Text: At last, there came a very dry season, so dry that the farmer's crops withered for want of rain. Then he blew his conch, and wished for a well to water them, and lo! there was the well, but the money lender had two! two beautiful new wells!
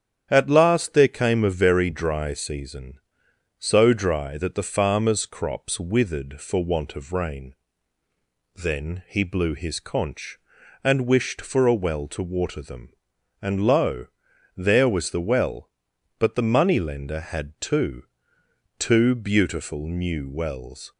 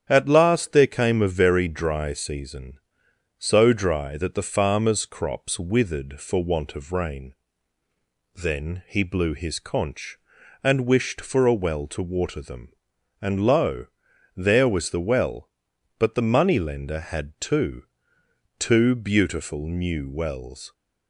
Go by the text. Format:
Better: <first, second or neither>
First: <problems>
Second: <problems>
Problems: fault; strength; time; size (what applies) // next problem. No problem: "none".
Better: neither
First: starts louder than the rest; strong; until 1.3 s; 9 dB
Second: starts louder than the rest; strong; until 1.1 s; 9.5 dB